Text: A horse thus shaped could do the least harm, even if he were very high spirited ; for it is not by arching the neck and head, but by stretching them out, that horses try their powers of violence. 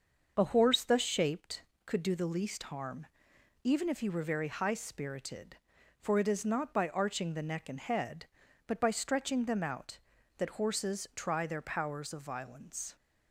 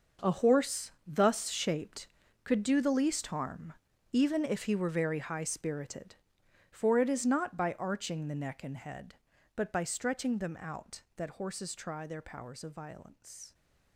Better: first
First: starts louder than the rest; until 1.3 s; 6.5 dB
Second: gets quieter; strong; throughout; 13.5 dB // starts louder than the rest; noticeable; until 1.3 s; 6 dB

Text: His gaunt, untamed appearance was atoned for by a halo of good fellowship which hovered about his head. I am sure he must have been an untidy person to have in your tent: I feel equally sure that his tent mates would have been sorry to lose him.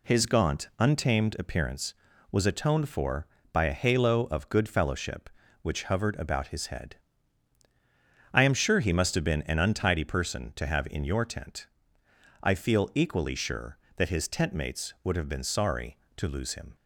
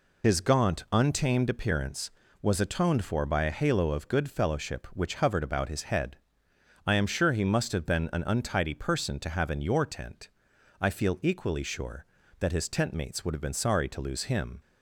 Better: first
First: none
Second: loses the start of "His"; at 0.2 s; 50 ms

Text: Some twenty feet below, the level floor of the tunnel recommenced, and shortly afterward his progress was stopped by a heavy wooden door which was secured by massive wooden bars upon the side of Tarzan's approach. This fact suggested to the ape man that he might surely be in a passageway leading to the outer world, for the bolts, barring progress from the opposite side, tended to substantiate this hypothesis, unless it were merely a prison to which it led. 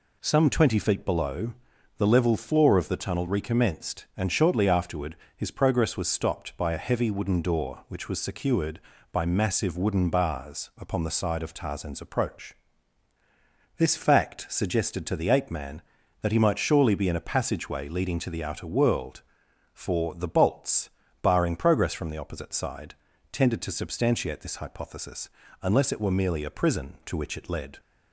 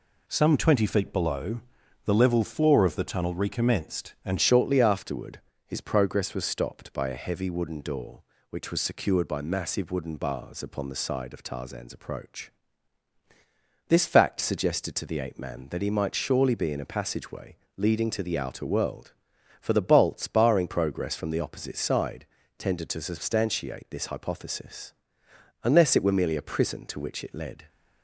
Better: first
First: pauses between "afterward" and "his"; slight; at 5.1 s; 0.22 s long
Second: changes voice at "shortly"; from 4.4 s on; 23.2 s long // pauses between "afterward" and "his"; slight; at 5.4 s; 0.26 s long // pauses between "passageway" and "leading"; slight; at 17.5 s; 0.20 s long

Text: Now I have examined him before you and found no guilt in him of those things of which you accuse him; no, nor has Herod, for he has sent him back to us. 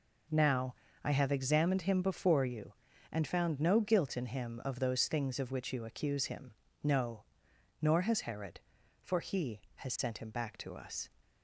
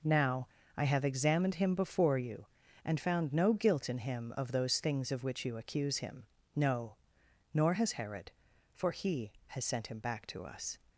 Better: neither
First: pauses between "Now" and "I"; slight; at 0.7 s; 0.28 s long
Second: pauses between "Now" and "I"; slight; at 0.4 s; 0.28 s long

